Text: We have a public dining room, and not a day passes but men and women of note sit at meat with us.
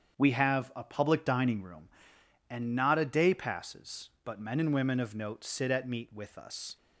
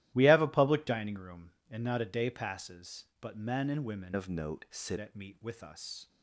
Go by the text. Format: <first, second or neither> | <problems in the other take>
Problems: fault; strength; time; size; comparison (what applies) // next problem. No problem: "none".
first | starts louder than the rest; strong; until 1.1 s; 14.5 dB; strong in the first // changes voice from "of" to "sit"; from 4.1 to 4.9 s; 0.8 s long